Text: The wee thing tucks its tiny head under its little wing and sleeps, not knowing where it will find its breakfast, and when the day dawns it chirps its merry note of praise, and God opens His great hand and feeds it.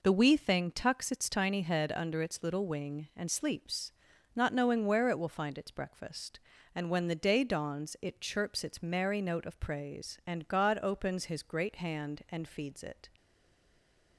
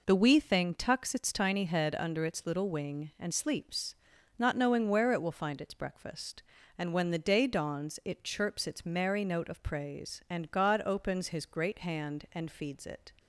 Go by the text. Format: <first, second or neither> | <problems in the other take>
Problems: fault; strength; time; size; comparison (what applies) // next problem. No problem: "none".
second | stays silent after the last word; from 13.1 s on; 1.0 s long